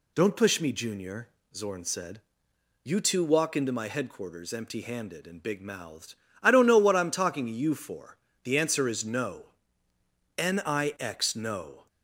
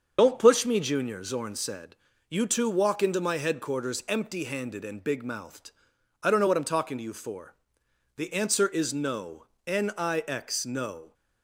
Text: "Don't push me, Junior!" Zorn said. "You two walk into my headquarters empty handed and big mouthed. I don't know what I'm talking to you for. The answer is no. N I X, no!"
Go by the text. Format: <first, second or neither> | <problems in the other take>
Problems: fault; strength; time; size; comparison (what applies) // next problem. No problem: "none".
first | loses the start of "Don't"; at 0.1 s; 60 ms // starts louder than the rest; until 1.1 s; 7 dB